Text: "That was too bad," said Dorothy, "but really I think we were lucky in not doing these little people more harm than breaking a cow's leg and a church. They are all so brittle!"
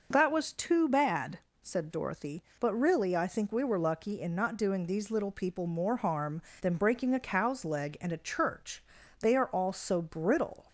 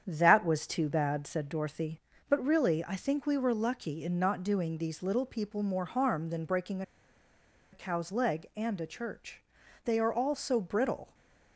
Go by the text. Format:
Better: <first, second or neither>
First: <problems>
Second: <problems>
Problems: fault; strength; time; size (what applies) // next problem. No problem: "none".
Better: first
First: none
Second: starts louder than the rest; strong; until 1.0 s; 8 dB // pauses between "breaking" and "a"; noticeable; at 6.8 s; 0.90 s long // stays silent after the last word; slight; from 11.0 s on; 0.5 s long